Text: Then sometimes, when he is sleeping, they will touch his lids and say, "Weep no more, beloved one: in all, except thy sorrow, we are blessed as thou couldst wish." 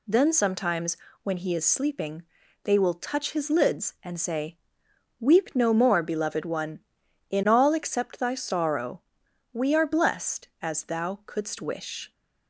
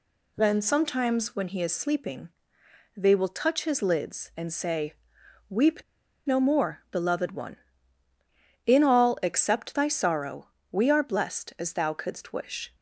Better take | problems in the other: first | pauses between "Weep" and "no"; at 5.8 s; 0.44 s long

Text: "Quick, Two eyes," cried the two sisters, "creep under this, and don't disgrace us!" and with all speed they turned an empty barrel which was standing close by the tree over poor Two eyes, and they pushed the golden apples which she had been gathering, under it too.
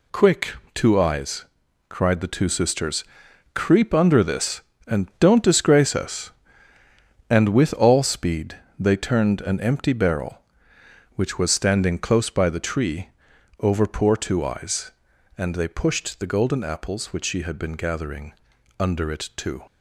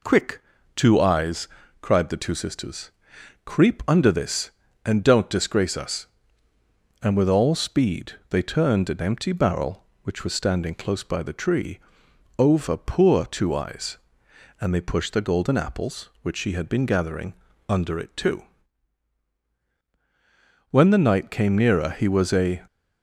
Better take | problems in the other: first | pauses between "speed" and "they"; slight; at 8.1 s; 0.16 s long; slight in the first // pauses between "tree" and "over"; noticeable; at 11.7 s; 0.58 s long; noticeable in the first // goes on to say "When the knight came nearer he was a"; strong; from 20.7 s on; 1.9 s long

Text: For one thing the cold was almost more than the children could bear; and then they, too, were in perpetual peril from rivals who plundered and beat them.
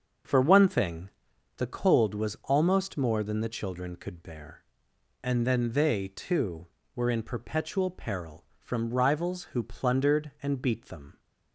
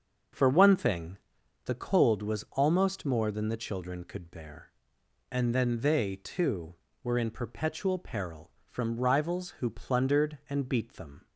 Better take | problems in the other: neither | starts louder than the rest; the same in both // pauses between "thing" and "the"; noticeable; the same in both

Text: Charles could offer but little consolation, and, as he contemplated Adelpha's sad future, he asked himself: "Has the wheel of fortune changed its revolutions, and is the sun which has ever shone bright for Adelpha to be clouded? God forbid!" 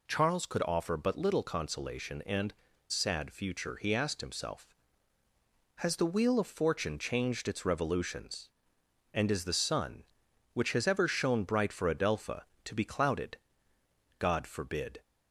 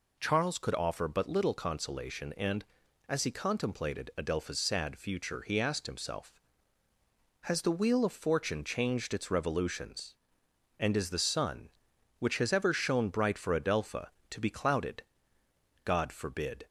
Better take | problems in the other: second | skips "as he contemplated Adelpha's"; at 2.7 s

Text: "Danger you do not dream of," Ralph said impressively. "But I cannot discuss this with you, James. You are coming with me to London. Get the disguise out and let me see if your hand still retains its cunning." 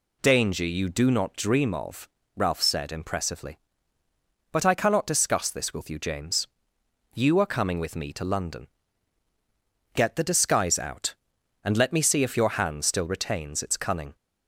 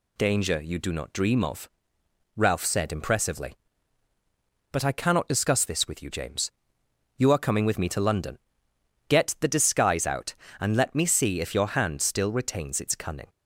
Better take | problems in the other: neither | none

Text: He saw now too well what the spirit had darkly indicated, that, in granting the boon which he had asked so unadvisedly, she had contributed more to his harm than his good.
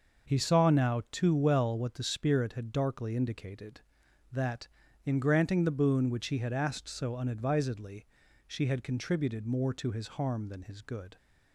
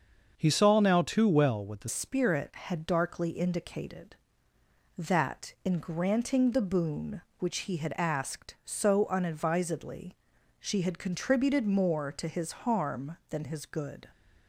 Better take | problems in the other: first | starts louder than the rest; until 1.3 s; 6.5 dB; noticeable in the first // changes voice at "spirit"; from 1.8 s on; 12.2 s long

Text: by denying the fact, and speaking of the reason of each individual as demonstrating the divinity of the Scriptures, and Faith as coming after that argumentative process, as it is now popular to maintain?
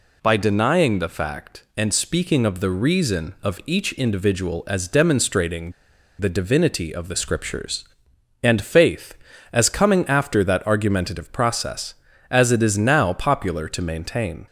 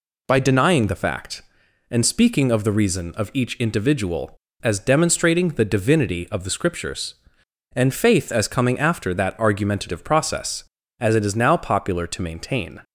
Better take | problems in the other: second | pauses between "demonstrating" and "the"; noticeable; at 5.7 s; 0.47 s long

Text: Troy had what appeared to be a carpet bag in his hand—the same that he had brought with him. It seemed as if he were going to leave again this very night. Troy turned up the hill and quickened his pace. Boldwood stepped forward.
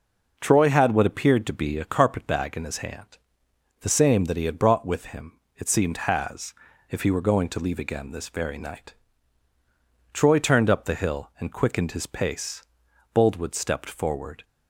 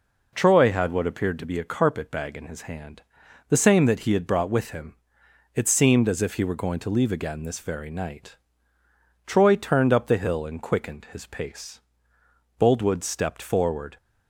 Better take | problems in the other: second | says "has" for "as"; at 5.9 s

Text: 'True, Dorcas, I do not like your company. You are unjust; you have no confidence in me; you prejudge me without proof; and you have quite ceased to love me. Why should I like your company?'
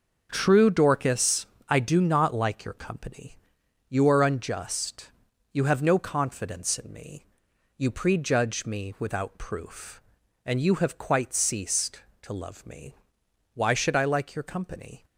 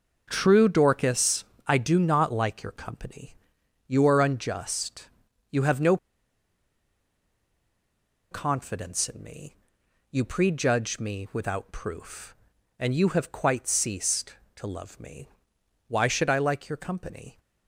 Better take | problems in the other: first | pauses between "no" and "confidence"; strong; at 5.9 s; 2.3 s long

